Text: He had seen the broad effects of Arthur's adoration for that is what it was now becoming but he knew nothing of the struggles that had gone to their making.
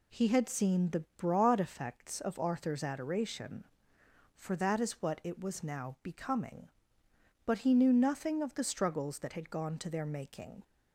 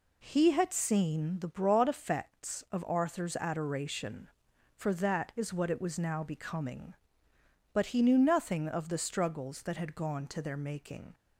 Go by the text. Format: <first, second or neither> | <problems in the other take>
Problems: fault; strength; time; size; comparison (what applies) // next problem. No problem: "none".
neither | none